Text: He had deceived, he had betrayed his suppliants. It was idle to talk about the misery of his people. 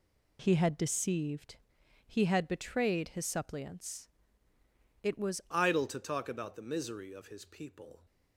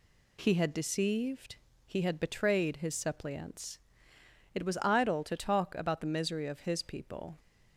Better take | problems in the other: second | changes voice at "idle"; from 5.5 s on; 2.5 s long

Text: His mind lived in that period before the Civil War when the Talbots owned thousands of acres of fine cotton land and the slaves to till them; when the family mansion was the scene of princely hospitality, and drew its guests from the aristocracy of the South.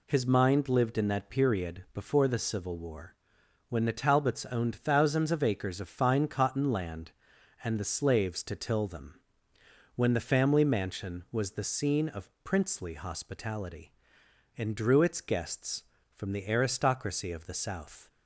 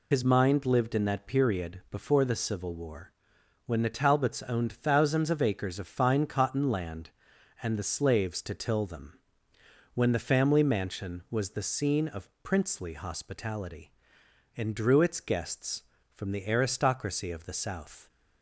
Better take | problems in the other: first | loses the start of "His"; at 0.1 s; 70 ms // pauses between "War" and "when"; noticeable; at 3.1 s; 0.54 s long; noticeable in the first

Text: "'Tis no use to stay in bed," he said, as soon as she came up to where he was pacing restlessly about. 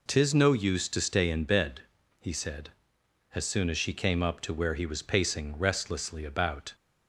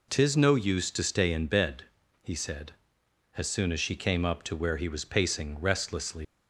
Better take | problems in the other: first | stops before "about"; at 6.2 s

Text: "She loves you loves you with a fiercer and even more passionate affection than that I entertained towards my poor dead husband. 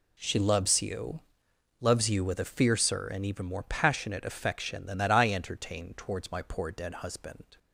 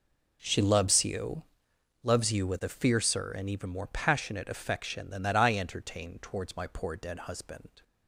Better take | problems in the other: first | starts louder than the rest; noticeable; until 1.4 s; 4.5 dB // pauses between "you" and "loves"; noticeable; at 1.4 s; 0.60 s long; noticeable in the first

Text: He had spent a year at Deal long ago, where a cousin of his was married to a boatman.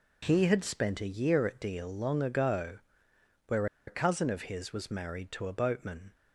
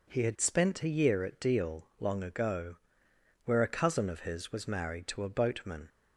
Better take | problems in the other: second | pauses between "where" and "a"; slight; at 3.6 s; 0.21 s long

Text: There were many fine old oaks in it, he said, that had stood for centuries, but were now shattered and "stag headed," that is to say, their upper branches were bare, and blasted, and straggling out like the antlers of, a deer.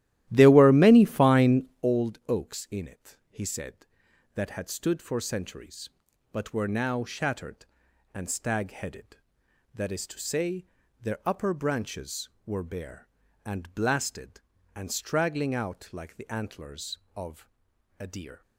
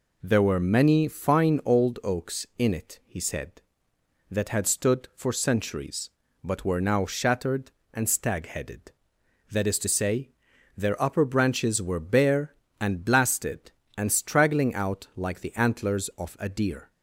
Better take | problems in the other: second | starts louder than the rest; strong; until 1.9 s; 14 dB // pauses between "fine" and "old"; slight; at 1.6 s; 0.18 s long

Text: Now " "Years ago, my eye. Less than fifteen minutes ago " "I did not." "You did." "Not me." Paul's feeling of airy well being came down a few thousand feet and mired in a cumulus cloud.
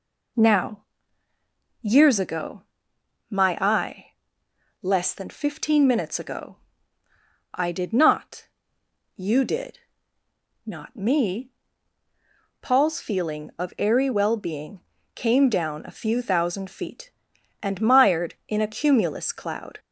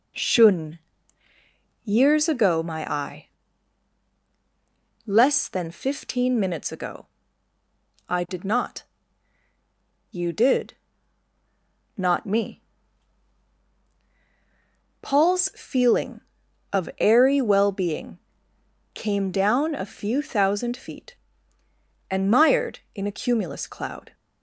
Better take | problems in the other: first | says "Shun" for "Now"; at 0.1 s // pauses between "being" and "came"; noticeable; at 18.1 s; 0.76 s long; slight in the first

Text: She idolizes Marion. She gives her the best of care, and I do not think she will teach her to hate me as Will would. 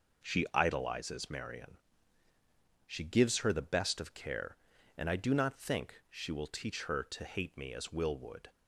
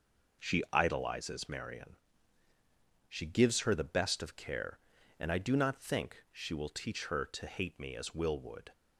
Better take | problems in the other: neither | none

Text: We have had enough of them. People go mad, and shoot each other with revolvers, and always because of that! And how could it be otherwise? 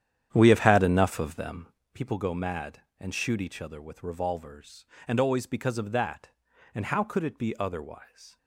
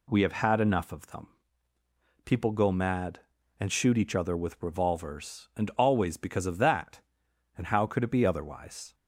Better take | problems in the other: second | starts louder than the rest; strong; until 1.8 s; 9.5 dB

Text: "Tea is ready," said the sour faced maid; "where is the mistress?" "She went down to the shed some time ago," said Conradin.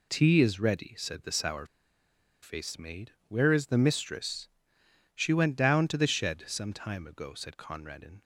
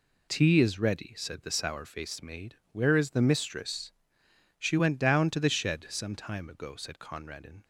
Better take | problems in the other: second | pauses between "sour" and "faced"; noticeable; at 1.6 s; 0.78 s long

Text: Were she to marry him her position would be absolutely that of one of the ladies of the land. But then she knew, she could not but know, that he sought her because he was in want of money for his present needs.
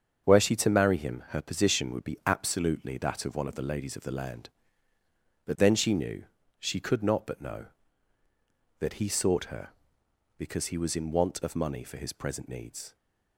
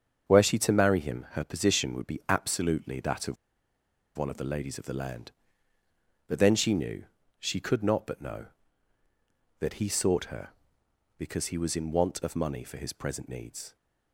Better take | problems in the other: first | starts louder than the rest; until 1.3 s; 7 dB; strong in the first // pauses between "of" and "one"; noticeable; at 3.3 s; 0.82 s long

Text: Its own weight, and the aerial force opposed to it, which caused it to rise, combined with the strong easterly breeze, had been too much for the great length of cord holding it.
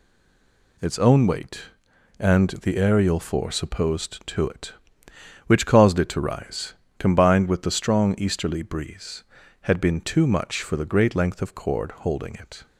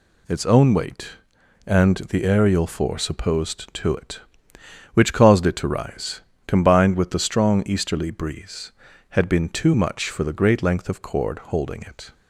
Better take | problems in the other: second | stays silent before the first word; slight; until 0.7 s; 0.7 s long

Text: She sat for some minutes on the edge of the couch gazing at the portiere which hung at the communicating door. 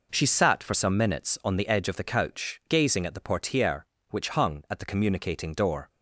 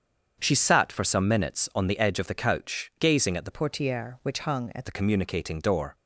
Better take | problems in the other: first | starts louder than the rest; strong; until 1.4 s; 7.5 dB // changes voice from "portiere" to "at"; from 3.5 to 4.8 s; 1.3 s long

